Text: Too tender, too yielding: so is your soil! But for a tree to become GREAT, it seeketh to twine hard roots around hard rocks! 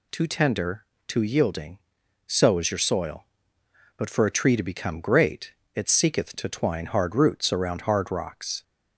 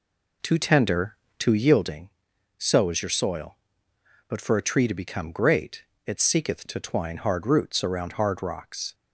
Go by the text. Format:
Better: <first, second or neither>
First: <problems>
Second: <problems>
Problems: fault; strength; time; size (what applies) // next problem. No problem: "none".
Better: first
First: none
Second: starts louder than the rest; slight; until 2.0 s; 3 dB